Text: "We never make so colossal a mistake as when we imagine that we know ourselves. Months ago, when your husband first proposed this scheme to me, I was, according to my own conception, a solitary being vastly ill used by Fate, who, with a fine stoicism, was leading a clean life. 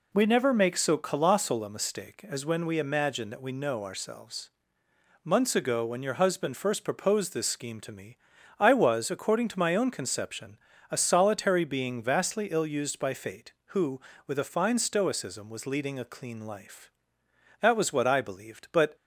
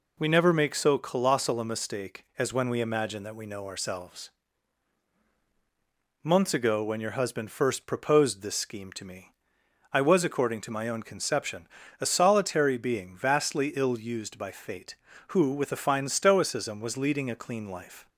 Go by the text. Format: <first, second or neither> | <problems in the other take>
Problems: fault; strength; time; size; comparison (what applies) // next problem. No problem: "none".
second | goes on to say "That was what I believed but"; from 17.6 s on; 1.3 s long